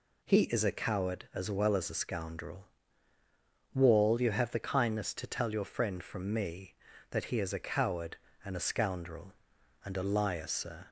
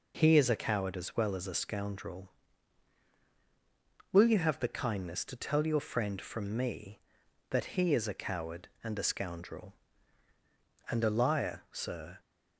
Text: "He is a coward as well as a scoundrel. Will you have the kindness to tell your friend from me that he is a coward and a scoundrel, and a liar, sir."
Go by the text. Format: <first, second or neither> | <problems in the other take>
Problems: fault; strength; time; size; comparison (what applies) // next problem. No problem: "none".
second | says "Wall" for "Will"; at 3.7 s